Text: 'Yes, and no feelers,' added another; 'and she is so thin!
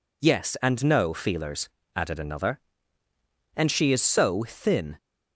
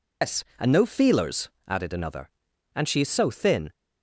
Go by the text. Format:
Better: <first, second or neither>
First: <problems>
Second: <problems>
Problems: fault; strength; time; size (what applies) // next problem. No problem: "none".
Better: first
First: none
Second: loses the start of "Yes"; at 0.2 s; 170 ms